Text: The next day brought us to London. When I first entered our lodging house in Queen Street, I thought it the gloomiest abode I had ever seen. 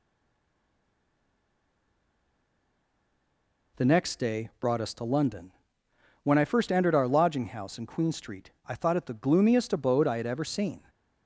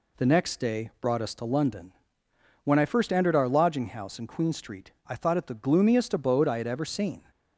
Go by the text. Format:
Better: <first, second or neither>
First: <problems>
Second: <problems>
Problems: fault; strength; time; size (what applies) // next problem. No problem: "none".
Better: second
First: stays silent before the first word; strong; until 3.7 s; 3.7 s long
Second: none